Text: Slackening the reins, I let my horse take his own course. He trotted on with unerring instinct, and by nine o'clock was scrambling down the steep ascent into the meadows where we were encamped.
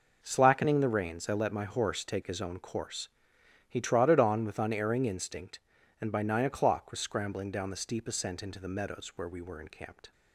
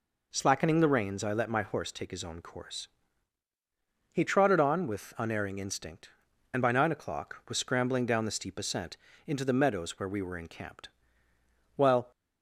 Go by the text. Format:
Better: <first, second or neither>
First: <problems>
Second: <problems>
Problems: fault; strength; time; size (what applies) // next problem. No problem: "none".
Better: first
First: none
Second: pauses between "ascent" and "into"; slight; at 8.9 s; 0.31 s long // goes on to say "While"; slight; from 11.7 s on; 0.34 s long